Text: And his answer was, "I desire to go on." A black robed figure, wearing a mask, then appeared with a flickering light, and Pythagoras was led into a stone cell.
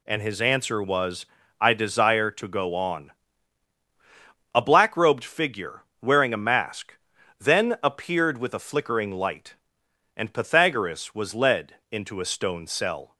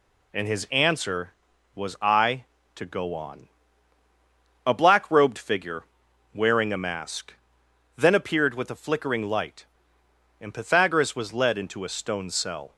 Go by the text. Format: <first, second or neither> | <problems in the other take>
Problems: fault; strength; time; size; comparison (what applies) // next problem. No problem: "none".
first | skips "desire"; at 2.5 s